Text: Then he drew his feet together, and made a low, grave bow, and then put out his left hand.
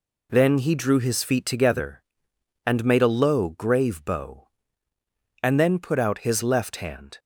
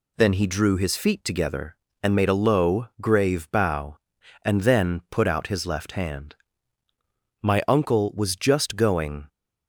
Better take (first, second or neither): first